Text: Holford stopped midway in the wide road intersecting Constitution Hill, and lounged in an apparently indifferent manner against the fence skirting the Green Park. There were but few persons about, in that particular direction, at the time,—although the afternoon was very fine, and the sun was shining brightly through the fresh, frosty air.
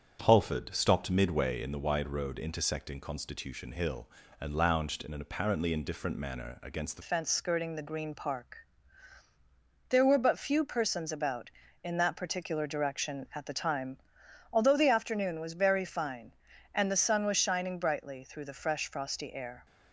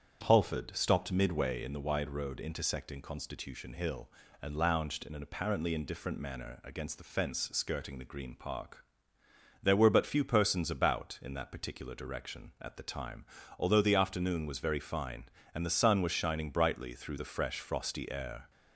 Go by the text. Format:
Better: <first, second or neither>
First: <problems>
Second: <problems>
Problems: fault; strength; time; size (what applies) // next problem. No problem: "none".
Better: second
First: starts louder than the rest; strong; until 1.2 s; 7.5 dB // changes voice at "fence"; from 7.0 s on; 12.6 s long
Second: starts louder than the rest; strong; until 1.2 s; 8 dB